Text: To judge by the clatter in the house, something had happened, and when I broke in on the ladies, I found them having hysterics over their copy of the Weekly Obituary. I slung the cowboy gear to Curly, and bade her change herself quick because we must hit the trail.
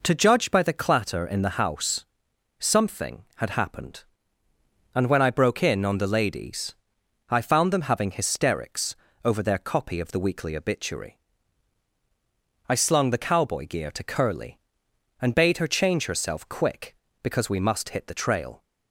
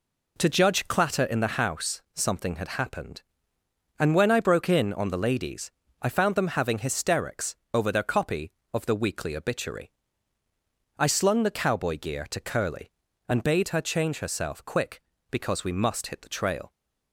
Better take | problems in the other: first | skips "by the"; at 0.8 s // pauses between "hysterics" and "over"; slight; at 7.5 s; 0.18 s long; slight in the first

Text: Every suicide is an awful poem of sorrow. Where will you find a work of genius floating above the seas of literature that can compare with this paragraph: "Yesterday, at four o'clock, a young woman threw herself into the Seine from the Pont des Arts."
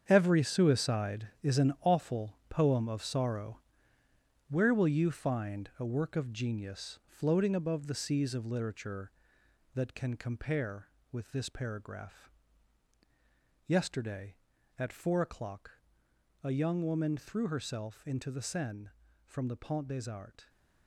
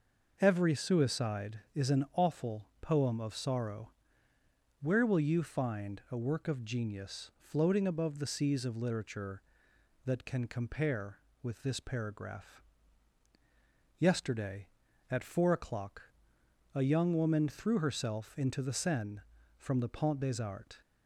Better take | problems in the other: second | gets quieter; strong; throughout; 10 dB

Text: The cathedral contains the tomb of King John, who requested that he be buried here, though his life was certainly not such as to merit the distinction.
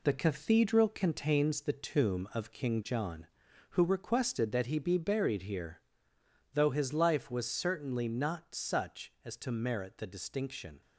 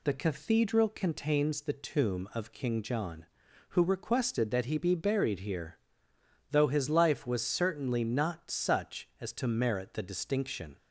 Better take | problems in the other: second | gets quieter; noticeable; throughout; 5.5 dB

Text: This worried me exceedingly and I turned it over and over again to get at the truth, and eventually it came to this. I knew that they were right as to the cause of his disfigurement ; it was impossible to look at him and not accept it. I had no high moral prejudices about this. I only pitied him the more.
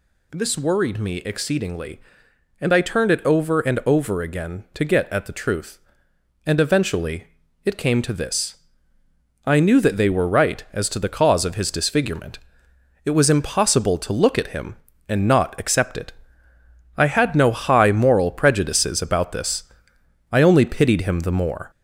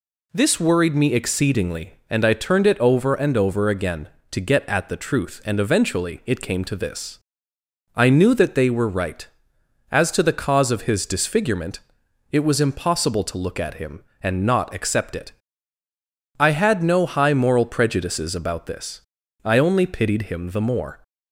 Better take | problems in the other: second | gets louder; throughout; 3.5 dB // pauses between "eventually" and "it"; at 7.2 s; 0.40 s long

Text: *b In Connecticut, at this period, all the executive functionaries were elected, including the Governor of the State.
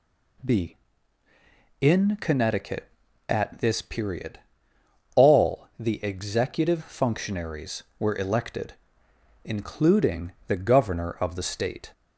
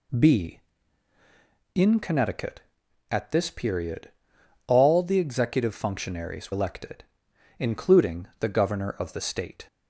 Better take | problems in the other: first | skips "were"; at 6.5 s

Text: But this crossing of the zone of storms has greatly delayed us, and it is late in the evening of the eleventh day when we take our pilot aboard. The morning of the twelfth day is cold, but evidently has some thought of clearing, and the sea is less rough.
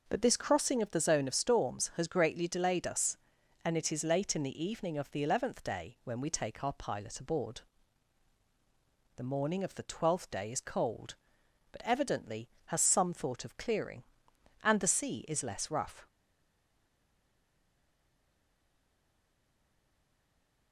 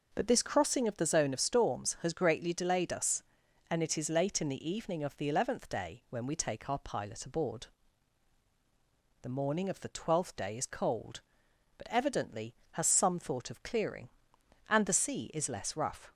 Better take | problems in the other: second | stays silent after the last word; strong; from 16.0 s on; 4.7 s long

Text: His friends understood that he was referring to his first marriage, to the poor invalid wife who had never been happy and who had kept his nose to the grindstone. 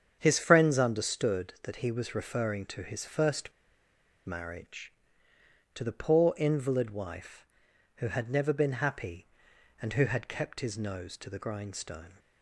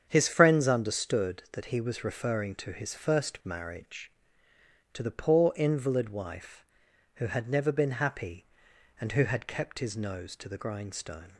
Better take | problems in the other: second | starts louder than the rest; strong; until 1.2 s; 8 dB; strong in the second // pauses between "first" and "marriage"; noticeable; at 3.5 s; 0.74 s long

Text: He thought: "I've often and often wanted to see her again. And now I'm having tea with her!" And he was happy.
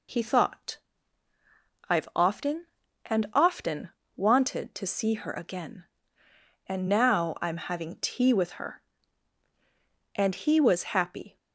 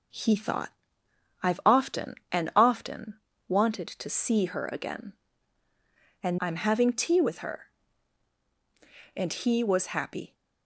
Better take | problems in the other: first | pauses between "often" and "wanted"; slight; at 3.1 s; 0.30 s long; slight in the first // skips "now"; at 6.3 s

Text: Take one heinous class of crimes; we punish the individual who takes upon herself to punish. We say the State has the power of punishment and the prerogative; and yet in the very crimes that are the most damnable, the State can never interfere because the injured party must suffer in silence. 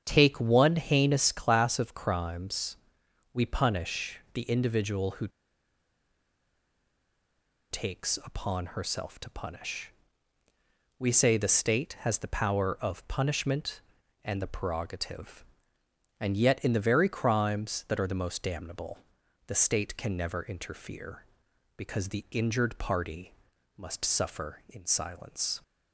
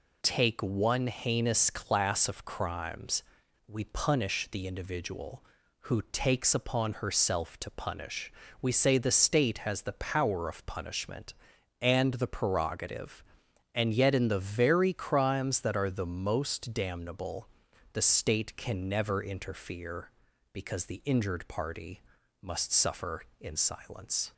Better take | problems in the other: second | starts louder than the rest; strong; until 1.0 s; 8 dB // pauses between "who" and "takes"; strong; at 5.2 s; 2.4 s long // pauses between "party" and "must"; at 23.3 s; 0.44 s long; also in the second

